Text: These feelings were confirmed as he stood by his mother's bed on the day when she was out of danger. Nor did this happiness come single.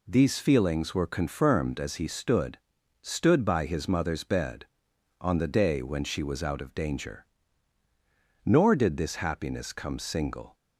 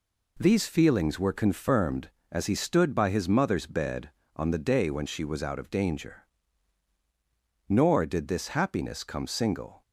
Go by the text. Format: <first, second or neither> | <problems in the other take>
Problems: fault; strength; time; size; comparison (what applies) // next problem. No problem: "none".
second | says "stood" twice; at 3.0 s